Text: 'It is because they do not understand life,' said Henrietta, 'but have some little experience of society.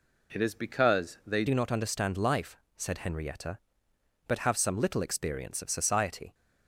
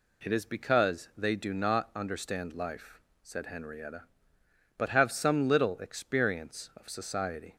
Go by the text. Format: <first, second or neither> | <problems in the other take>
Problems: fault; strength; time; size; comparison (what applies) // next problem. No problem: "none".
second | changes voice at "do"; from 1.4 s on; 4.9 s long